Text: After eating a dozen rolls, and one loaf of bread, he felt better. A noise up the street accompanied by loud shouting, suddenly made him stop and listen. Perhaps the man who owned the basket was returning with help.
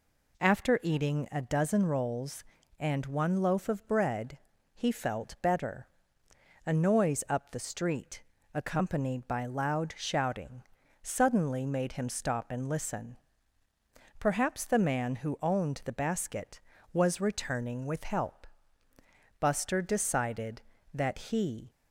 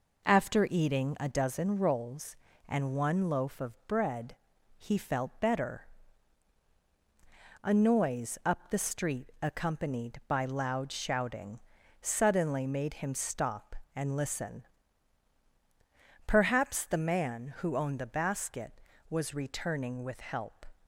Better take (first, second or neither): second